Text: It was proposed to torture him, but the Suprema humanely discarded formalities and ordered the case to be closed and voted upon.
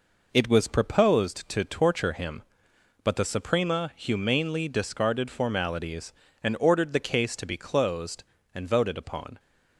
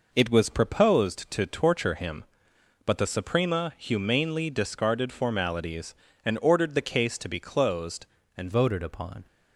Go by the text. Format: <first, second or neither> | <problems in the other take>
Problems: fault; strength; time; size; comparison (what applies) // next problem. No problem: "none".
first | changes voice at "voted"; from 8.5 s on; 0.7 s long